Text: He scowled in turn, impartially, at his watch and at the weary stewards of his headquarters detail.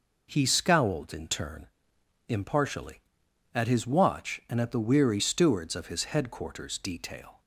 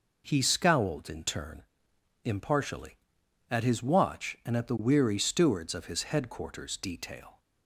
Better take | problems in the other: neither | none

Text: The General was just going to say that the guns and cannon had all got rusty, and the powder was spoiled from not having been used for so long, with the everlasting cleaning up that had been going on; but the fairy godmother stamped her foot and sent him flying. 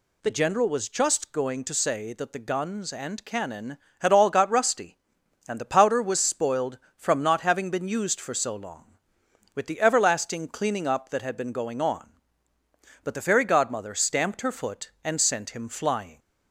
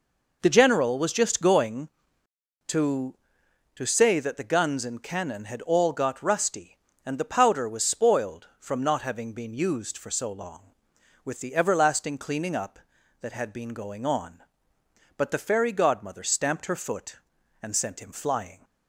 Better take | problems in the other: first | says "to" twice; at 3.7 s

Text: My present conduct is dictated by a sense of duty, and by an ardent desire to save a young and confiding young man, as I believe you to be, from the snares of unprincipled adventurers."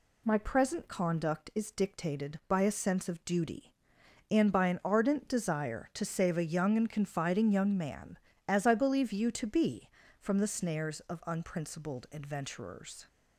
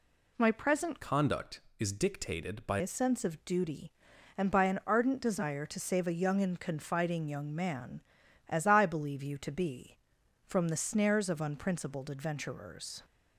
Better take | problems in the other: first | changes voice from "conduct" to "by"; from 1.0 to 2.7 s; 1.7 s long

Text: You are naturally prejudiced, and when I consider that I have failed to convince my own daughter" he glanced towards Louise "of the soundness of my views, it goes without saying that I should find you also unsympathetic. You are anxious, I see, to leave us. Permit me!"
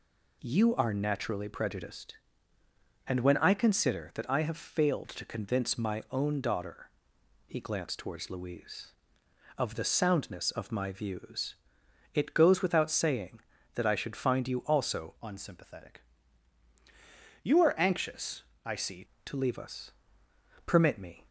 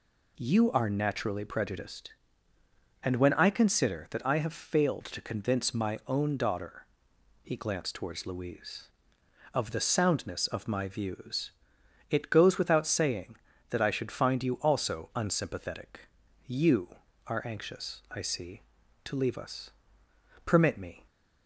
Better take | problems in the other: second | pauses between "daughter" and "he"; noticeable; at 6.8 s; 0.58 s long; noticeable in the second // changes voice from "unsympathetic" to "see"; from 15.2 to 19.0 s; 3.8 s long

